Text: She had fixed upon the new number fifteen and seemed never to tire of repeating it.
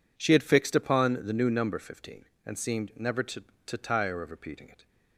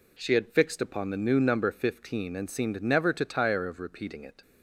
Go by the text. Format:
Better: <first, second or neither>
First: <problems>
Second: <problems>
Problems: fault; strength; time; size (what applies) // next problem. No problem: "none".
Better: second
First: says "to" twice; at 3.6 s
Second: none